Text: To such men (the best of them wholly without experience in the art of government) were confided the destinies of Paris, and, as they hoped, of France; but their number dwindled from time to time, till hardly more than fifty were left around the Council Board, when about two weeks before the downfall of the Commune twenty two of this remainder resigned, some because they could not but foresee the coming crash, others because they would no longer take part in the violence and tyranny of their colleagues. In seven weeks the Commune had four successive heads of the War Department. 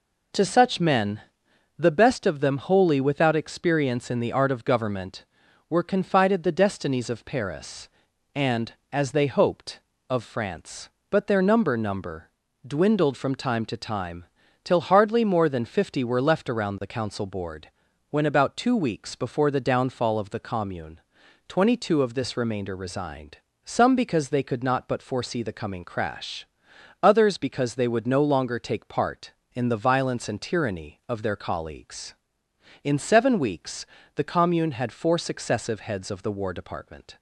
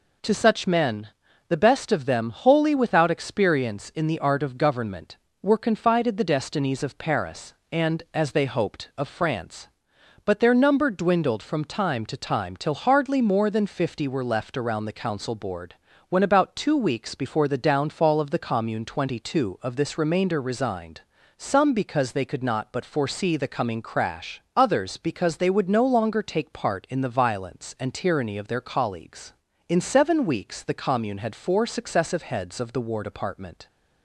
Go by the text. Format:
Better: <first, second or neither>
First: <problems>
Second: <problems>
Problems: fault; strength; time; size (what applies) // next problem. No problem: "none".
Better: second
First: says "number" twice; at 11.7 s // pauses between "Commune" and "twenty"; noticeable; at 20.9 s; 0.48 s long // pauses between "weeks" and "the"; slight; at 33.8 s; 0.30 s long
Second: none